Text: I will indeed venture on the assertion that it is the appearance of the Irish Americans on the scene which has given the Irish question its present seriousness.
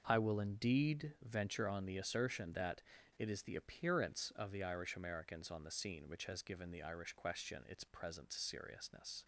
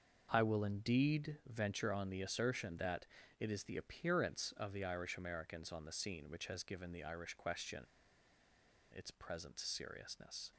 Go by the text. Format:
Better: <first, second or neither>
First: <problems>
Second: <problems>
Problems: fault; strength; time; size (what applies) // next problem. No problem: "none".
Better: first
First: starts louder than the rest; noticeable; until 1.0 s; 6 dB // pauses between "that" and "it"; at 2.8 s; 0.37 s long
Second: starts louder than the rest; noticeable; until 1.3 s; 6 dB // pauses between "that" and "it"; slight; at 3.0 s; 0.34 s long // pauses between "question" and "its"; at 7.8 s; 1.1 s long